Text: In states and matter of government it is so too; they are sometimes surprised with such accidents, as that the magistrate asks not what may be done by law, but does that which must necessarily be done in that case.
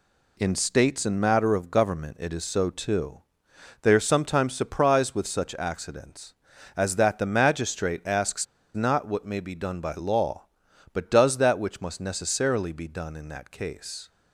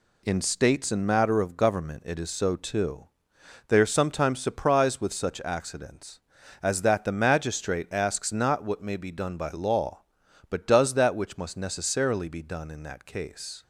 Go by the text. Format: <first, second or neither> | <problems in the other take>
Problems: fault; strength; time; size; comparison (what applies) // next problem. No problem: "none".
second | pauses between "asks" and "not"; slight; at 8.4 s; 0.29 s long